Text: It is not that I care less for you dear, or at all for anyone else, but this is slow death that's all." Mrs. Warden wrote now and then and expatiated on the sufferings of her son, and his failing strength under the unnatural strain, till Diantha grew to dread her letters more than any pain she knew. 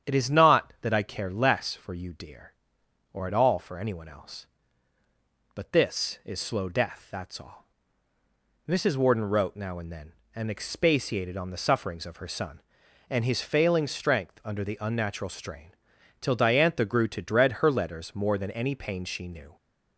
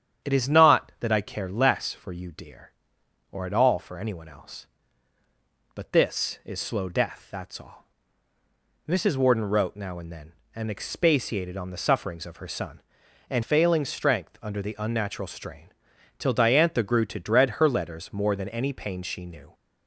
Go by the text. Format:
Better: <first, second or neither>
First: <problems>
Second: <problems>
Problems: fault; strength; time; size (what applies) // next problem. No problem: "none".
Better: first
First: starts louder than the rest; strong; until 1.1 s; 8.5 dB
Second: starts louder than the rest; strong; until 1.3 s; 8.5 dB // skips "his"; at 13.4 s